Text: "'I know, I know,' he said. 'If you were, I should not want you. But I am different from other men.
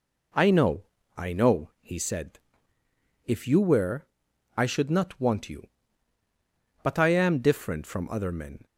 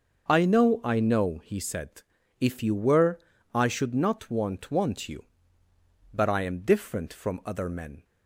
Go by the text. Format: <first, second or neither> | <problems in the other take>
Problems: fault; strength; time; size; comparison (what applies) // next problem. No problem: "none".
first | starts louder than the rest; until 1.3 s; 6 dB // says "want" twice; at 4.6 s